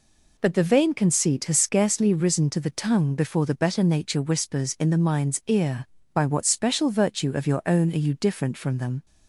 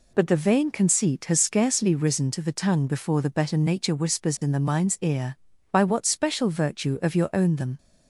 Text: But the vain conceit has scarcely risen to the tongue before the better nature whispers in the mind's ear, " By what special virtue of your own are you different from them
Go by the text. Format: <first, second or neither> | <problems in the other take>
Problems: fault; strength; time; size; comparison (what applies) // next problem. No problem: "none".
first | skips "are you different from"; at 7.5 s